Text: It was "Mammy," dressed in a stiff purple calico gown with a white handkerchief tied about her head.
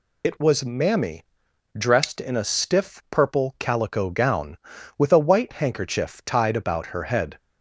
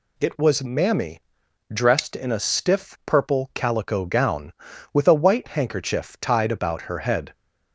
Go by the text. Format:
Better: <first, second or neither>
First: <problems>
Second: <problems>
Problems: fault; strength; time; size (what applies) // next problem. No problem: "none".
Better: second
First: loses the start of "It"; at 0.2 s; 50 ms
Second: none